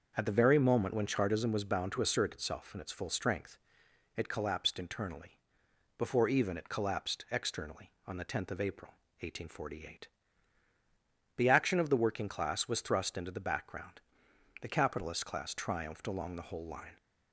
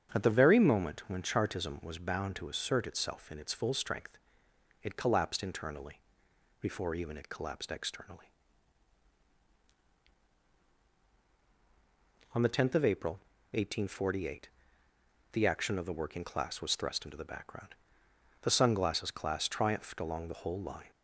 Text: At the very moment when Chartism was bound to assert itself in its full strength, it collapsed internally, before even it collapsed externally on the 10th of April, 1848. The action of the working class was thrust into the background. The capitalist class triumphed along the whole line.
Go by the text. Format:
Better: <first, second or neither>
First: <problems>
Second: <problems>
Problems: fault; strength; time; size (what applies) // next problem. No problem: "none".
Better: first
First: starts louder than the rest; until 1.1 s; 6 dB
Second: starts louder than the rest; strong; until 1.1 s; 8 dB // says "sunglasses" for "capitalist"; at 18.4 s